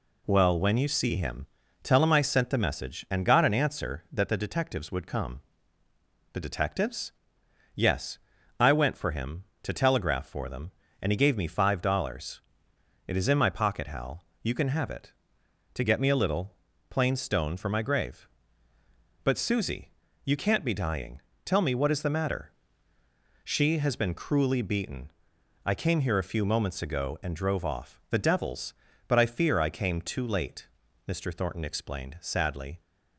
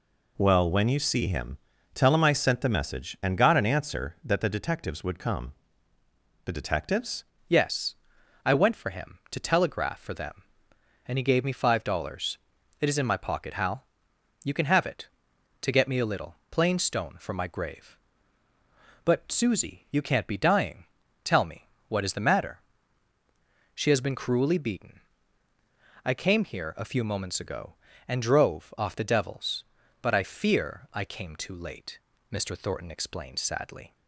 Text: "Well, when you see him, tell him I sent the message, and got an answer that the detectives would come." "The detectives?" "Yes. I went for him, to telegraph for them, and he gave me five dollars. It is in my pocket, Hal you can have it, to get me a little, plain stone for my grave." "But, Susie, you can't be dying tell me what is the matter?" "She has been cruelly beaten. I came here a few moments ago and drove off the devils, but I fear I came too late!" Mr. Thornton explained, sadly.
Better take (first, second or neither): first